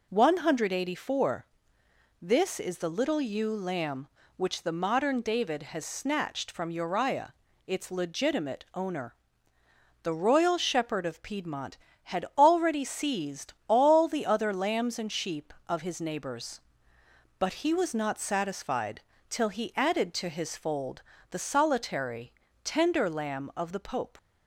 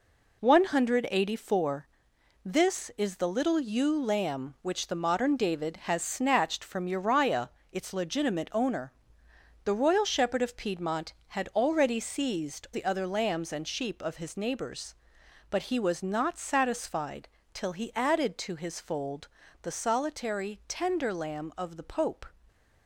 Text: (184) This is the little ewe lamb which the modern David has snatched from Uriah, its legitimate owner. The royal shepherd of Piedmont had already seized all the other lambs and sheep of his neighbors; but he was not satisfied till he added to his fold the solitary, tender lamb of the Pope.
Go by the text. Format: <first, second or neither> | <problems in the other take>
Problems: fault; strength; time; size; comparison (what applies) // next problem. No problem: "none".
first | skips "all"; at 12.6 s // pauses between "satisfied" and "till"; slight; at 17.2 s; 0.24 s long; slight in the first // pauses between "fold" and "the"; slight; at 19.2 s; 0.34 s long; slight in the first